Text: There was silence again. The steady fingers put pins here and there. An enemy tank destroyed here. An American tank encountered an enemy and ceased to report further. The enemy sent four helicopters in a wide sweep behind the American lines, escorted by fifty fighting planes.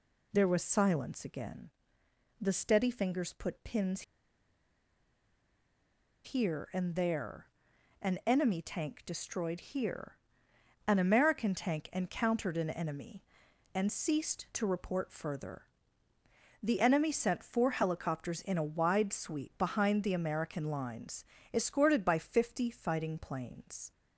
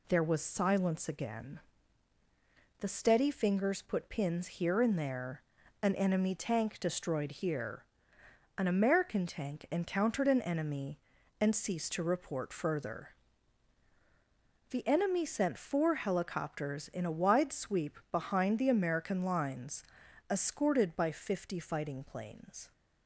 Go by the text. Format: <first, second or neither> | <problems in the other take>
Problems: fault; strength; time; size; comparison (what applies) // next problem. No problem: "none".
second | pauses between "pins" and "here"; strong; at 4.0 s; 2.2 s long